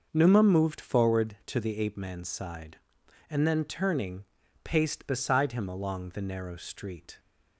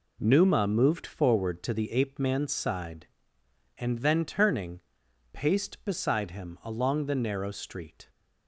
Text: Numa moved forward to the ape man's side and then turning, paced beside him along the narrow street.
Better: neither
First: none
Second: none

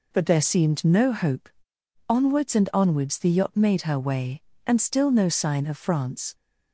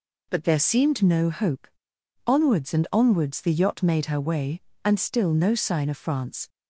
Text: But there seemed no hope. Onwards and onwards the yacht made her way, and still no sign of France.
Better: neither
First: none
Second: none

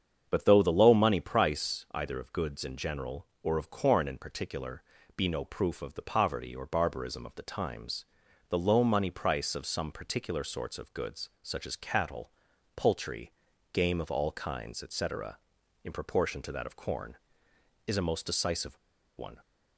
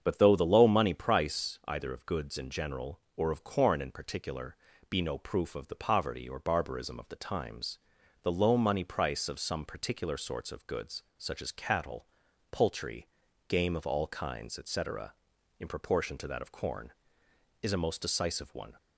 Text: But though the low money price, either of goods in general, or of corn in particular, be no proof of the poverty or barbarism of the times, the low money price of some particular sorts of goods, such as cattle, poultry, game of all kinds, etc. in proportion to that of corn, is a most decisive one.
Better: second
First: starts louder than the rest; strong; until 1.3 s; 7.5 dB // pauses between "decisive" and "one"; at 18.7 s; 0.39 s long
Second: starts louder than the rest; strong; until 1.0 s; 7.5 dB

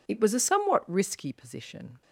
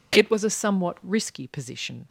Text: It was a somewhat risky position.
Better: neither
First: none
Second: none

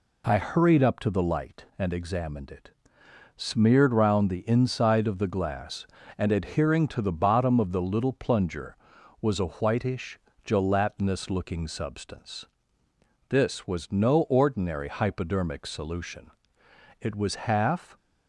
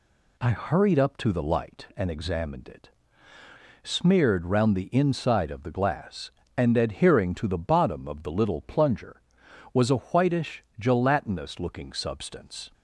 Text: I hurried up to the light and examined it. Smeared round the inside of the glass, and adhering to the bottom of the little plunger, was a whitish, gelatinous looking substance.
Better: second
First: goes on to say "This was no ordinary hypodermic solution It was half"; strong; from 13.2 s on; 4.6 s long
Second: none

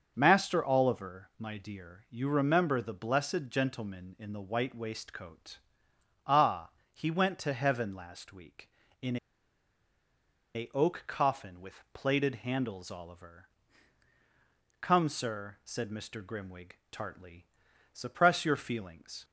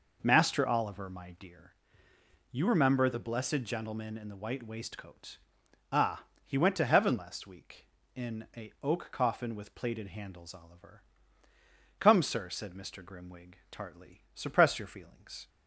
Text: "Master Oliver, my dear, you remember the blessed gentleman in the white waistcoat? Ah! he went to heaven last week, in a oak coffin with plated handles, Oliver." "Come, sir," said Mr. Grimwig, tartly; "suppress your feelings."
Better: second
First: starts louder than the rest; until 1.1 s; 6.5 dB // pauses between "in" and "a"; strong; at 9.1 s; 1.3 s long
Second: none

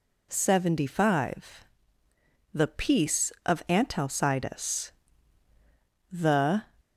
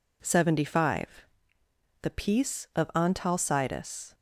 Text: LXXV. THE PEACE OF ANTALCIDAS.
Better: second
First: goes on to say "The"; from 6.1 s on; 0.50 s long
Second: none

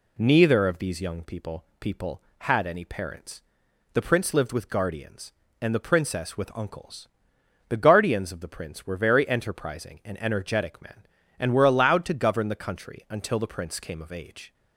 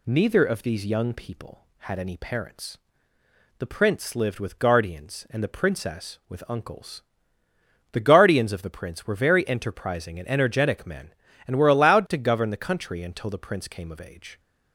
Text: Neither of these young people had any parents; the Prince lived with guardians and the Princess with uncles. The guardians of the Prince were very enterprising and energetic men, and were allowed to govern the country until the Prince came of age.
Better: second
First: says "people" twice; at 1.7 s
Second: none

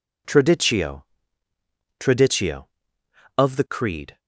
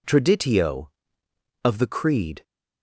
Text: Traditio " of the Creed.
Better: second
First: says "Traditio" twice; at 1.9 s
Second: none

